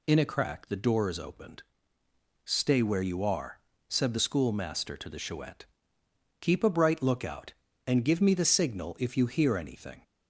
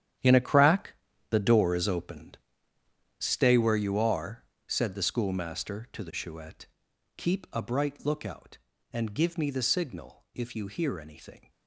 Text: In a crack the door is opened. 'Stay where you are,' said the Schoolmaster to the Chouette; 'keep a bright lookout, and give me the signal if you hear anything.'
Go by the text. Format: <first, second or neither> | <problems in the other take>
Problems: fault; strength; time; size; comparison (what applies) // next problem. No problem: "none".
first | gets quieter; strong; throughout; 13 dB // pauses between "crack" and "the"; slight; at 0.9 s; 0.36 s long